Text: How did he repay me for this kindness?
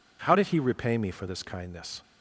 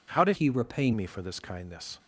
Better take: first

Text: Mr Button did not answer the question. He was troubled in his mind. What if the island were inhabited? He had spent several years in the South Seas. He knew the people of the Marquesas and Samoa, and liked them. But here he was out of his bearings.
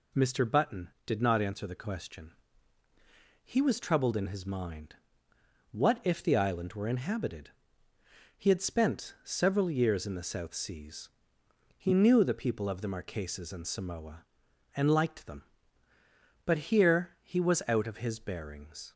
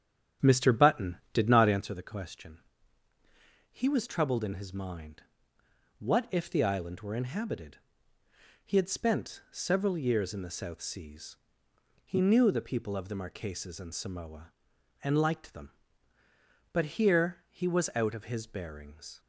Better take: first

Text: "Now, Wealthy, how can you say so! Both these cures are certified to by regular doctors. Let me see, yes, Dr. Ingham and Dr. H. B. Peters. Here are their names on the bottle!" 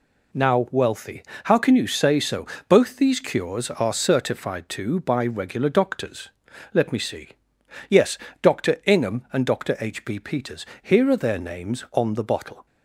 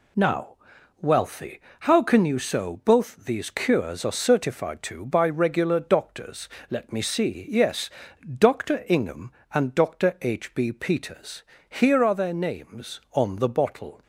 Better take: first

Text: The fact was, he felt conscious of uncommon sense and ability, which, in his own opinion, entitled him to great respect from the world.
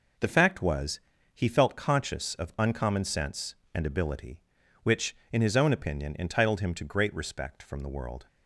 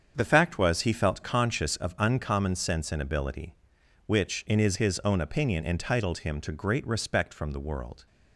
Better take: first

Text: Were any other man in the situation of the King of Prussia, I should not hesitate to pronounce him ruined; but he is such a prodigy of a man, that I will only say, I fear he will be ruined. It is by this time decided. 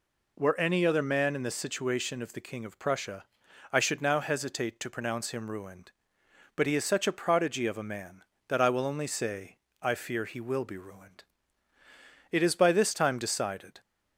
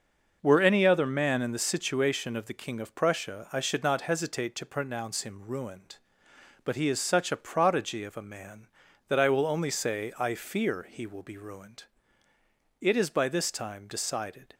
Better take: second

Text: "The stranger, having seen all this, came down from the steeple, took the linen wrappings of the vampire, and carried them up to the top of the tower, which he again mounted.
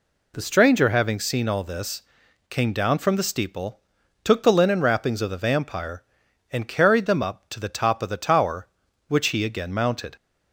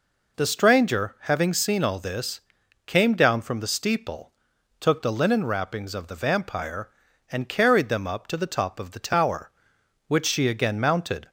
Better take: first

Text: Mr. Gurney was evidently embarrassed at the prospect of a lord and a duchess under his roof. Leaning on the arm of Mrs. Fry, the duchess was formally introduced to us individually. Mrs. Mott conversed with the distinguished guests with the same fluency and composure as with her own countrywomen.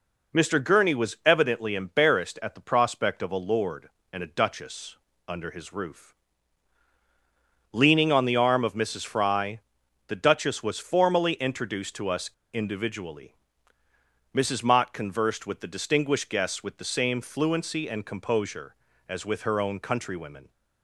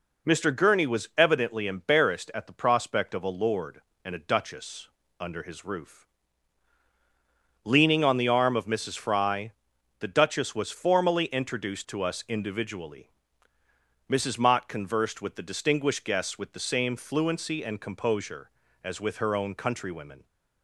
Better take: second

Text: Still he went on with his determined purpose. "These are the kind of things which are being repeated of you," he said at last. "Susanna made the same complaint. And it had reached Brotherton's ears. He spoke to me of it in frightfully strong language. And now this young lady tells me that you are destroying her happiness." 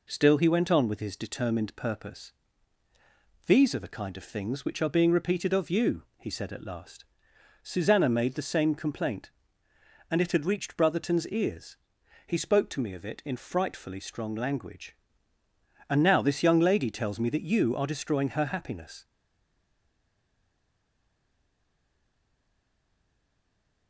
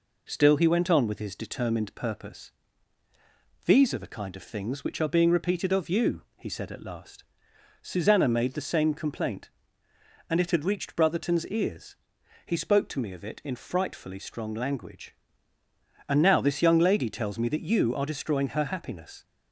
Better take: second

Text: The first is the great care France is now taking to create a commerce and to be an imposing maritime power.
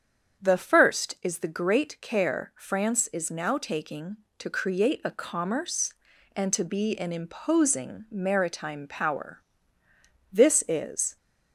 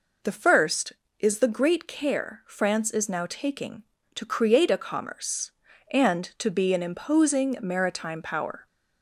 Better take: second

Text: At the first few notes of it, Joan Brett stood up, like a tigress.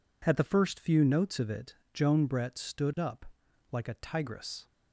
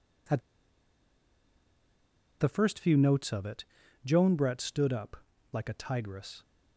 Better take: first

